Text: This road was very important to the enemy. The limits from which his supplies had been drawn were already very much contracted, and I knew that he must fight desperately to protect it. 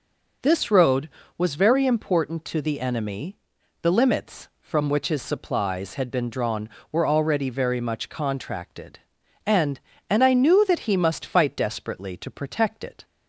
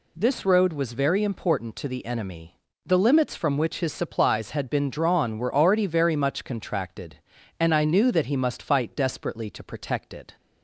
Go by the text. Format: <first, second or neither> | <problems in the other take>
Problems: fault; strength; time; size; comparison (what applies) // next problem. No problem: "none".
second | says "and" twice; at 10.0 s